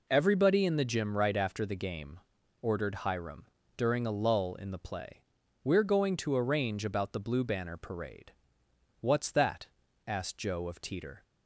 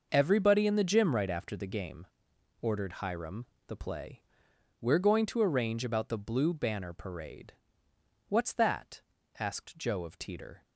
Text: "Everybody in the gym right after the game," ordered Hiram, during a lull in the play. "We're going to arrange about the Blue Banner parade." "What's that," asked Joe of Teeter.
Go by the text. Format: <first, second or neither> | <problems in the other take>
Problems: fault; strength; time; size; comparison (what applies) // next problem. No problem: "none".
first | skips "during a lull in"; at 3.5 s